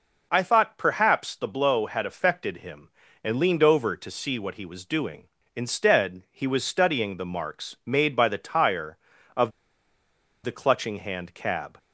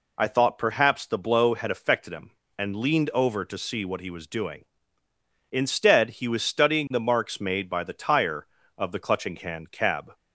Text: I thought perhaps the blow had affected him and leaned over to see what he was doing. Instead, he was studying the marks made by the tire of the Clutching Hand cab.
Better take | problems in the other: second | pauses between "of" and "the"; noticeable; at 9.5 s; 0.92 s long

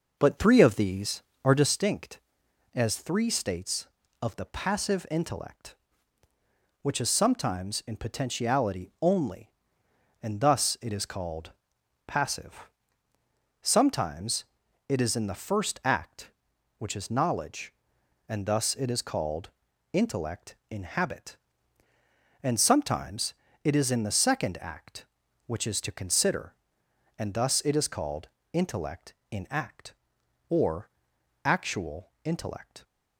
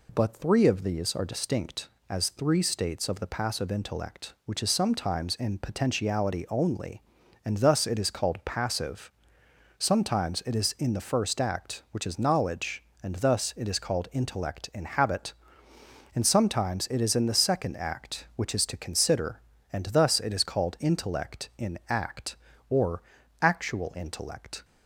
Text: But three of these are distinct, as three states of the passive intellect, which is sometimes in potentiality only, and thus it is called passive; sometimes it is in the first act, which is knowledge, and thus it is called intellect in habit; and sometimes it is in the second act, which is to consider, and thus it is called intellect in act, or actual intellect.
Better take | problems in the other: second | starts louder than the rest; noticeable; until 1.8 s; 5.5 dB // pauses between "called" and "passive"; noticeable; at 11.5 s; 0.56 s long // pauses between "sometimes" and "it"; at 14.4 s; 0.44 s long // pauses between "called" and "intellect"; at 19.4 s; 0.44 s long // pauses between "sometimes" and "it"; slight; at 23.3 s; 0.28 s long // pauses between "called" and "intellect"; slight; at 28.2 s; 0.24 s long // pauses between "or" and "actual"; noticeable; at 30.8 s; 0.54 s long; also in the second

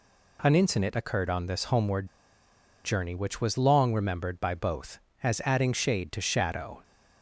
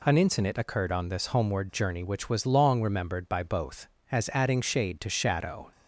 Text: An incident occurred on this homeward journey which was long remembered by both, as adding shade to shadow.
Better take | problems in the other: second | pauses between "homeward" and "journey"; noticeable; at 2.0 s; 0.78 s long

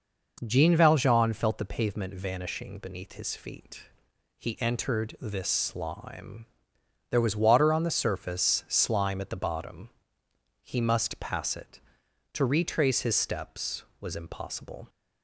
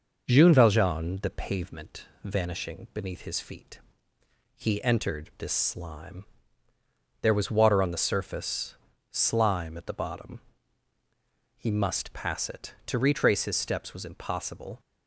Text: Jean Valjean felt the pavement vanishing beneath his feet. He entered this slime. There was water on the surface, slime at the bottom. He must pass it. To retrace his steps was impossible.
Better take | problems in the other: first | skips "felt"; at 1.2 s // pauses between "pavement" and "vanishing"; slight; at 2.0 s; 0.16 s long

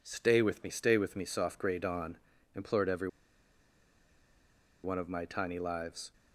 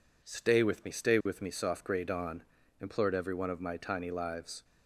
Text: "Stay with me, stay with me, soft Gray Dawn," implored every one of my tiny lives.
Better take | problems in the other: second | pauses between "every" and "one"; strong; at 3.0 s; 1.7 s long

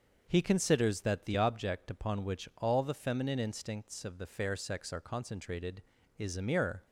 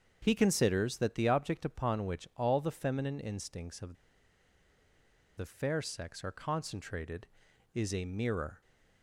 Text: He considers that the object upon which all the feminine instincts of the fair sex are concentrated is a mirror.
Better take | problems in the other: first | starts louder than the rest; until 1.2 s; 7 dB; also in the first // pauses between "of" and "the"; strong; at 3.9 s; 1.4 s long

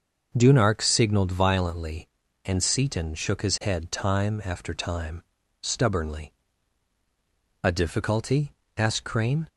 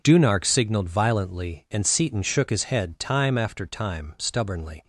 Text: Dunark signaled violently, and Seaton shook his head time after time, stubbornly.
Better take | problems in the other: second | starts louder than the rest; noticeable; until 1.3 s; 6 dB // goes on to say "A difficulty asked Crane"; strong; from 7.6 s on; 1.8 s long

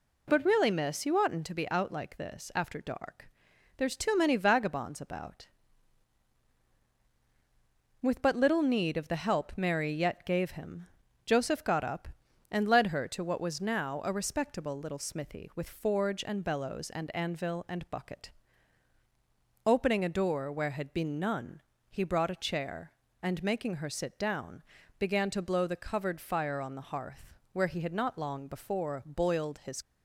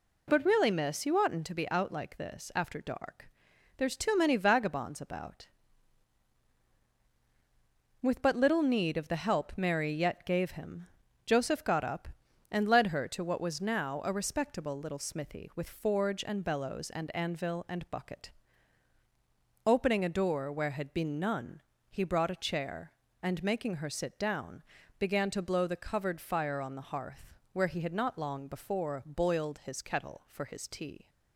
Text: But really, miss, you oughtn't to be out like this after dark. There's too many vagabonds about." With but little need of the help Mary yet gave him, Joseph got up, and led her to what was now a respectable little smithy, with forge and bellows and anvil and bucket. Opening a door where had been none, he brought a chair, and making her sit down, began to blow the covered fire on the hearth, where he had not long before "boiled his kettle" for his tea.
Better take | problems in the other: second | stops before "kettle for his tea"; at 29.8 s

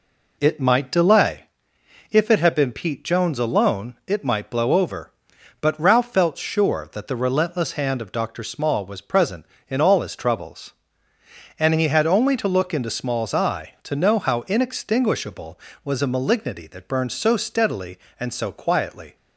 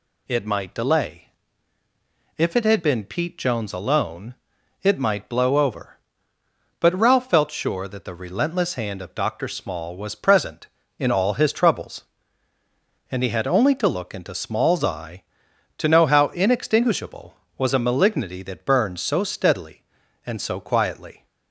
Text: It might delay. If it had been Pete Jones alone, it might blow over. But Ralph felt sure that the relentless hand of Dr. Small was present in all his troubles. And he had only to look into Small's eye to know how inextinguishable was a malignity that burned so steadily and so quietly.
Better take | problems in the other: second | starts louder than the rest; until 1.5 s; 3.5 dB

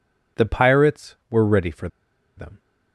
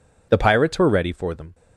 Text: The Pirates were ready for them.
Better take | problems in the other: second | pauses between "for" and "them"; noticeable; at 1.8 s; 0.48 s long

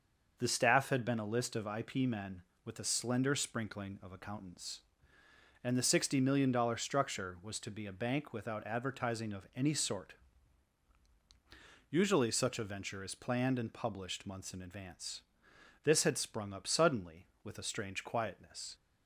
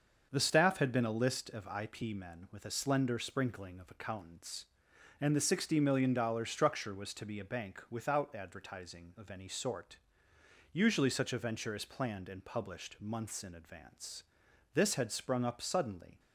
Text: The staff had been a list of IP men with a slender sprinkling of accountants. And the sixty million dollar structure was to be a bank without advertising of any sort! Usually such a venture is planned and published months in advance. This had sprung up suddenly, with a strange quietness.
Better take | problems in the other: first | starts louder than the rest; until 1.3 s; 6.5 dB; also in the first // stops before "with a strange quietness"; at 16.1 s

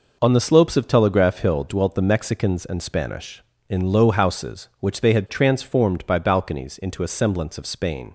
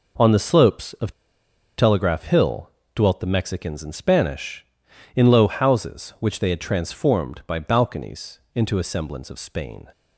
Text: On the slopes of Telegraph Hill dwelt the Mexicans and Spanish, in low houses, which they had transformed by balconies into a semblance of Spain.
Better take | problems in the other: first | pauses between "of" and "Telegraph"; noticeable; at 1.1 s; 0.67 s long // pauses between "Hill" and "dwelt"; slight; at 2.7 s; 0.24 s long // pauses between "balconies" and "into"; slight; at 8.3 s; 0.16 s long

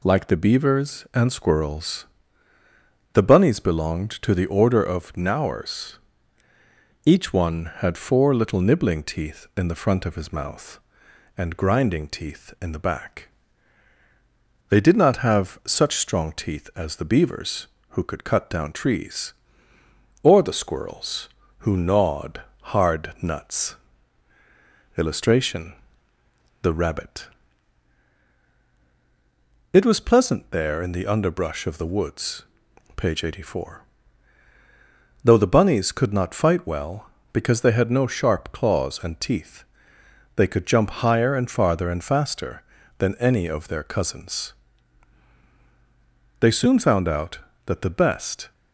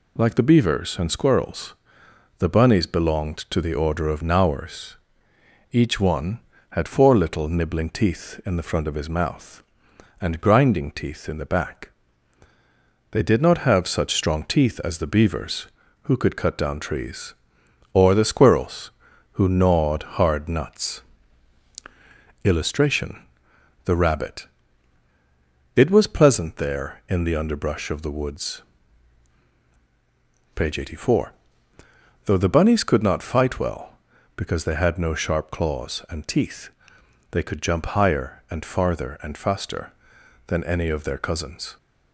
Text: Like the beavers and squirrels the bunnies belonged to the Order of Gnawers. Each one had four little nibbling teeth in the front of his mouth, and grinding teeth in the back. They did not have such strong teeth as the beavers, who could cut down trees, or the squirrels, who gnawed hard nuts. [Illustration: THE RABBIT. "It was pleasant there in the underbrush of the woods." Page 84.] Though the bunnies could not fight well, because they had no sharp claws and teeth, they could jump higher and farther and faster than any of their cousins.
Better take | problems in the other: second | pauses between "squirrels" and "the"; at 2.0 s; 1.0 s long; noticeable in the second // pauses between "gnawed" and "hard"; slight; at 22.3 s; 0.32 s long // goes on to say "They soon found out that the best"; strong; from 46.3 s on; 2.1 s long

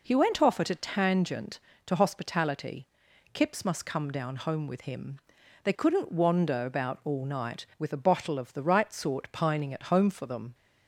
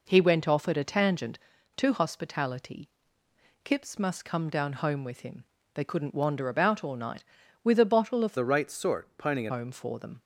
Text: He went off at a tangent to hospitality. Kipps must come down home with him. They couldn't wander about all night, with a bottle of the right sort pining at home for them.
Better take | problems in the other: first | changes voice from "the" to "at"; from 8.3 to 9.5 s; 1.2 s long

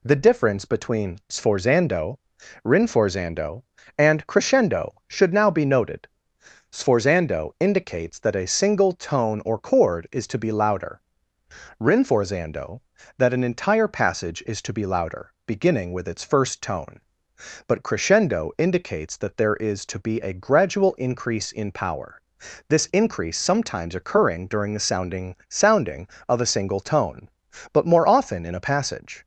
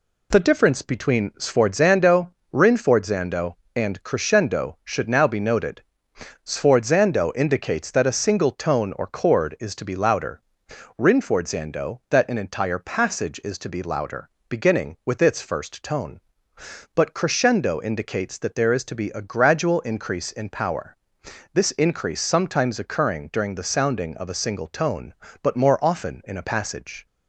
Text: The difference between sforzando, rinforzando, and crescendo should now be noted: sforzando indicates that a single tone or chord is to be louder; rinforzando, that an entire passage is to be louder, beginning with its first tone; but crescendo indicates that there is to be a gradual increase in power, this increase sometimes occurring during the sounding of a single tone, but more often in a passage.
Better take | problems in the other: second | says "sounding" twice; at 25.4 s

